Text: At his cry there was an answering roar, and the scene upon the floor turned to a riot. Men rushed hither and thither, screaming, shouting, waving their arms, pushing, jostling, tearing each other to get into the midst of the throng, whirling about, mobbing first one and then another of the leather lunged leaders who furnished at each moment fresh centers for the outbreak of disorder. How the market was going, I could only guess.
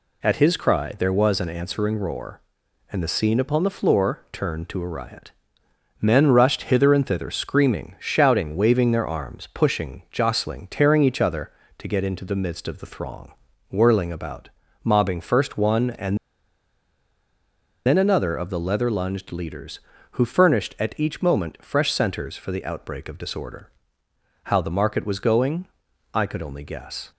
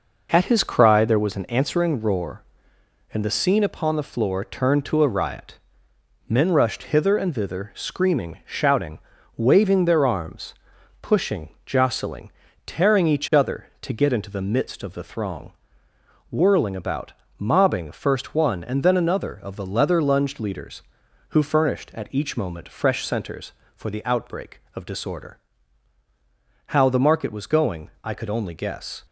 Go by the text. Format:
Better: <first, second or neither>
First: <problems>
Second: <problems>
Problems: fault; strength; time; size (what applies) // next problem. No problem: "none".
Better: second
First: pauses between "and" and "then"; strong; at 16.1 s; 1.6 s long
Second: none